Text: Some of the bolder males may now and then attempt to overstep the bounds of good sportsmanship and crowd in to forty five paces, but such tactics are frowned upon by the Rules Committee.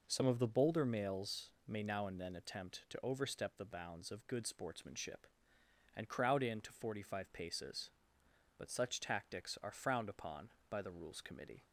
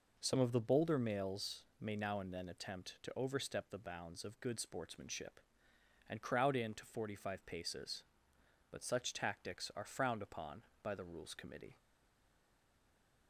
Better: first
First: pauses between "males" and "may"; slight; at 1.4 s; 0.16 s long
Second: pauses between "males" and "may"; slight; at 1.6 s; 0.16 s long // stays silent after the last word; noticeable; from 11.7 s on; 1.5 s long

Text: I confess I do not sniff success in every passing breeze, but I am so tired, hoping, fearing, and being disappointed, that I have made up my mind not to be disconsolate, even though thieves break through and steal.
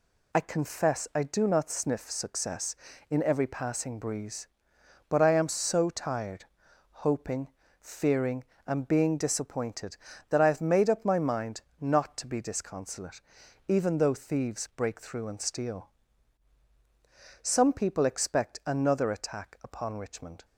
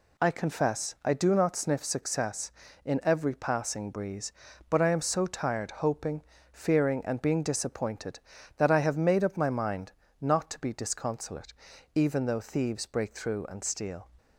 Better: second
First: pauses between "mind" and "not"; slight; at 11.6 s; 0.18 s long // goes on to say "Some people expect another attack upon Richmond"; strong; from 17.4 s on; 3.0 s long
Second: pauses between "mind" and "not"; slight; at 9.9 s; 0.28 s long

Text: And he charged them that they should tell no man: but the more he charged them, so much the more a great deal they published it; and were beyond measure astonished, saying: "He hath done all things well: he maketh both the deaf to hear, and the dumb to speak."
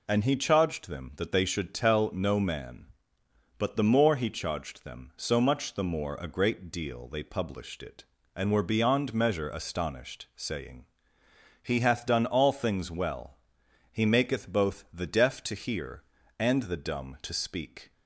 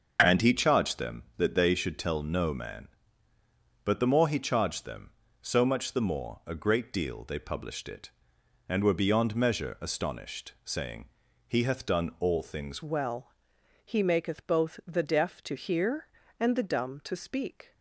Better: first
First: none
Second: changes voice at "well"; from 12.8 s on; 4.9 s long

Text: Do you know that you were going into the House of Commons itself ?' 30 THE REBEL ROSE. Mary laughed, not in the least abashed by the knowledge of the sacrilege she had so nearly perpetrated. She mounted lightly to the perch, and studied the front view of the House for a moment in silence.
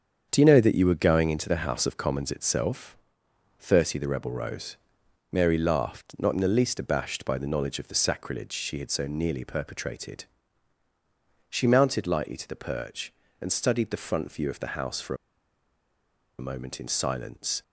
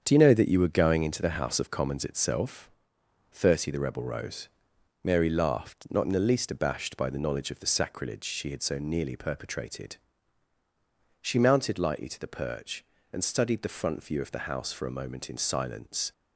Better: second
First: starts louder than the rest; until 1.3 s; 6.5 dB // pauses between "for" and "a"; at 15.1 s; 1.2 s long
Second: starts louder than the rest; until 1.0 s; 6.5 dB

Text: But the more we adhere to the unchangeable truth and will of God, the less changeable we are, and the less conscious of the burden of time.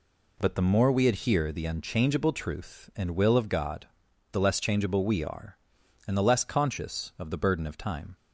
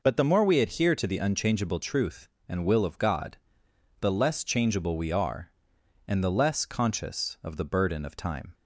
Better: second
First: skips "to"; at 1.5 s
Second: none

